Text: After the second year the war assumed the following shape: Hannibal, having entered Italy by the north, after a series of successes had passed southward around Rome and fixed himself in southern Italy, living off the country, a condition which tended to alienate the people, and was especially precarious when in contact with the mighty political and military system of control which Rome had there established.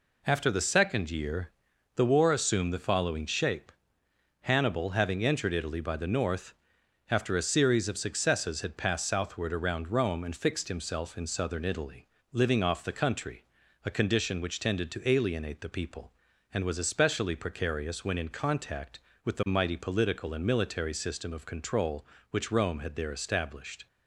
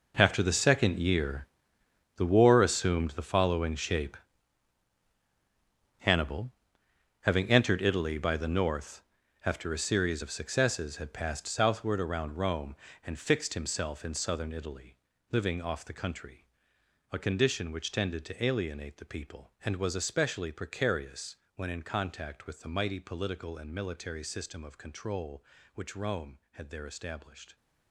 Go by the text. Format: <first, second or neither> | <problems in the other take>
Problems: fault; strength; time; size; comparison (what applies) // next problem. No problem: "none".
first | gets quieter; strong; throughout; 14.5 dB // pauses between "year" and "the"; noticeable; at 1.4 s; 0.70 s long; noticeable in the first // pauses between "precarious" and "when"; slight; at 21.3 s; 0.18 s long